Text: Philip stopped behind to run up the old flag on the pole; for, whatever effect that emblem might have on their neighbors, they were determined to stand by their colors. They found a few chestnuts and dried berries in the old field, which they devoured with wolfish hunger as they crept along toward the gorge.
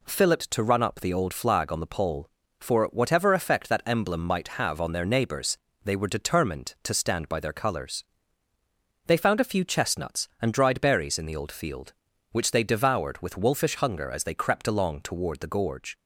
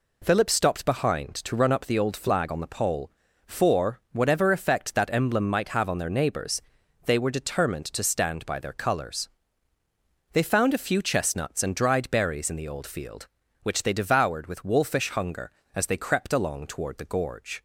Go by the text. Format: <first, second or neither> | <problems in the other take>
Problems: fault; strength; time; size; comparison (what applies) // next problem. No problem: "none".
second | skips "stopped behind"; at 0.4 s